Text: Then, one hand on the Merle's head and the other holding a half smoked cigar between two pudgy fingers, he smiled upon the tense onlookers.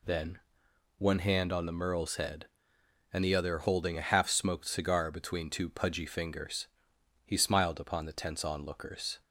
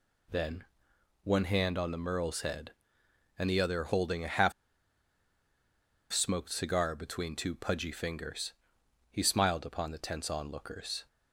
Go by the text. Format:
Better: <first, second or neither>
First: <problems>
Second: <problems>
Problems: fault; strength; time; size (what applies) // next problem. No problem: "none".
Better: first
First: none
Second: pauses between "half" and "smoked"; strong; at 4.5 s; 1.6 s long